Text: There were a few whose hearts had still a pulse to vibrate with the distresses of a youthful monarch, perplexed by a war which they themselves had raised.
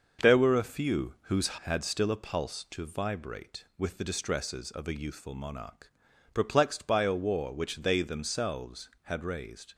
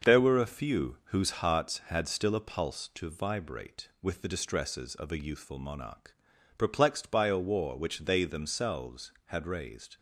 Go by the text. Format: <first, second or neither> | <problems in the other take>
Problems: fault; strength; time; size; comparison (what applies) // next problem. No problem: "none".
second | starts louder than the rest; noticeable; until 1.3 s; 6 dB; noticeable in the second // skips "hearts"; at 1.5 s